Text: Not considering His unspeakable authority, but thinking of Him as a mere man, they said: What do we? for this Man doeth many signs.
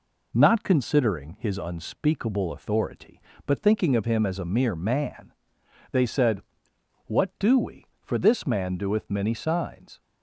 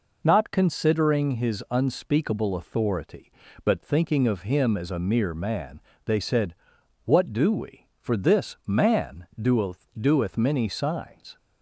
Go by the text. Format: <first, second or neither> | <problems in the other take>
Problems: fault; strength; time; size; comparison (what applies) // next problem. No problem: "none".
first | says "doeth" twice; at 9.9 s